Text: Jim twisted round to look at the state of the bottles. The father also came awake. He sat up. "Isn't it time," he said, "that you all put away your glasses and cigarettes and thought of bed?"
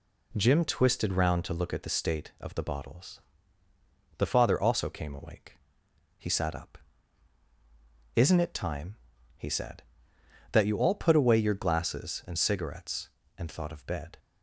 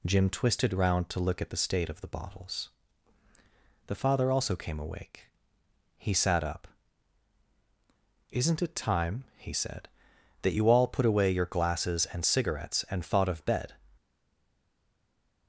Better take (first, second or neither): first